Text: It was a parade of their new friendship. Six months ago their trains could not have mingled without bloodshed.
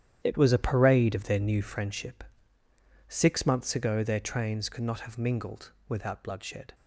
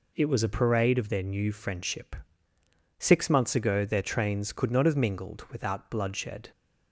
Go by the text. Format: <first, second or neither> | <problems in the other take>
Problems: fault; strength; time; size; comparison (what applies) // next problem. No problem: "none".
second | gets quieter; strong; throughout; 11.5 dB // pauses between "mingled" and "without"; slight; at 5.7 s; 0.16 s long